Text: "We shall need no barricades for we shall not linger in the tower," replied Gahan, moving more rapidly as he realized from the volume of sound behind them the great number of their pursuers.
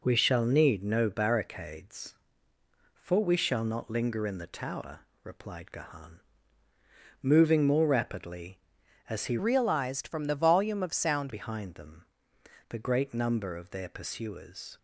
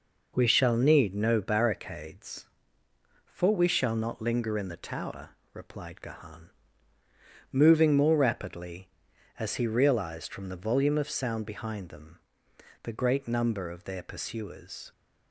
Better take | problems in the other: second | changes voice from "realized" to "sound"; from 9.3 to 11.3 s; 2.0 s long // pauses between "them" and "the"; noticeable; at 12.0 s; 0.64 s long; noticeable in the second

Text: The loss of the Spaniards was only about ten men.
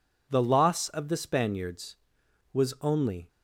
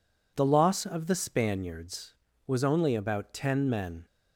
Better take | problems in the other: second | stops before "about ten men"; at 3.2 s

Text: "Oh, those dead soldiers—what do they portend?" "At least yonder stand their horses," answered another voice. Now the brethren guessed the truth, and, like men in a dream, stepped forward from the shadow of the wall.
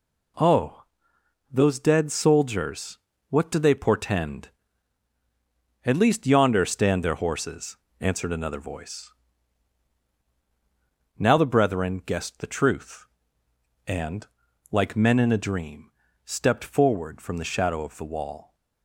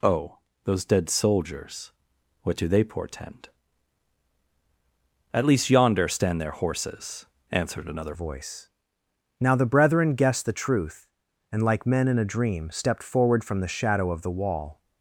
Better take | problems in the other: first | changes voice at "voice"; from 8.1 s on; 6.6 s long

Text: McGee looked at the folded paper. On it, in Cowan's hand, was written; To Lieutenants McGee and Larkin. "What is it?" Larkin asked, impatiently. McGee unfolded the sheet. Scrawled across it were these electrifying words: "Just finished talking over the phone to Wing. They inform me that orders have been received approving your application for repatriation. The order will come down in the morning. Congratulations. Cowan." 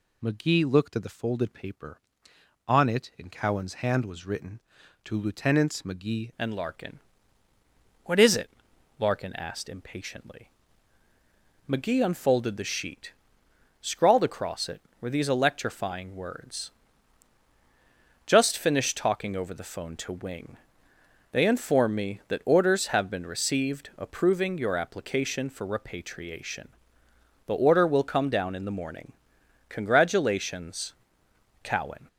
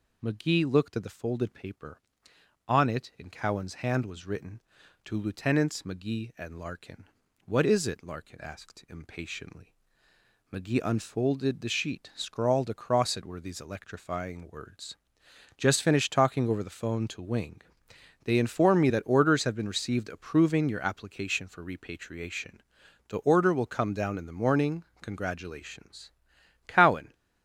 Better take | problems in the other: second | changes voice at "and"; from 6.3 s on; 25.7 s long

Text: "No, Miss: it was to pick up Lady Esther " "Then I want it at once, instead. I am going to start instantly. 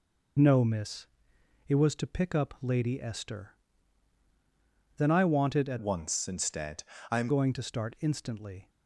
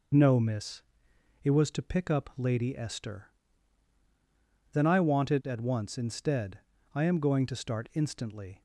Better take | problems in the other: second | changes voice from "once" to "am"; from 5.7 to 7.2 s; 1.5 s long

